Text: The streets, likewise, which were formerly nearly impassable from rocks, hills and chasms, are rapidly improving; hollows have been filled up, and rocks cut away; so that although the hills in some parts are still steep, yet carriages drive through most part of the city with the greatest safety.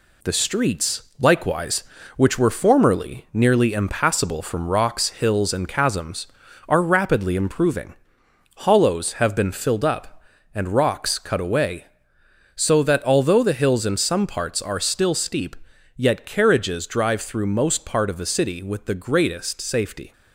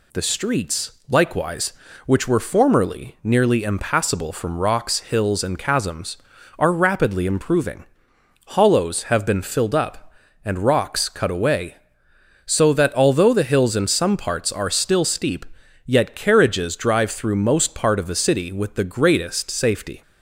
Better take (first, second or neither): second